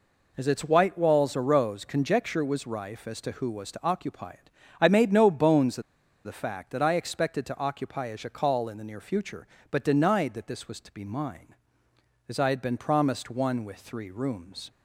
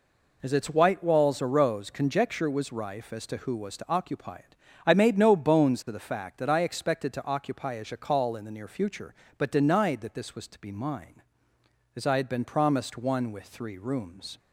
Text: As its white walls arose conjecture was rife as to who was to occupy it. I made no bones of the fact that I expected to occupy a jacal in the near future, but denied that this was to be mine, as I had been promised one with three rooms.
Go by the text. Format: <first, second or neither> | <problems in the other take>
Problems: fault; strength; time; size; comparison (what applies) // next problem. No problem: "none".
second | pauses between "of" and "the"; at 5.8 s; 0.44 s long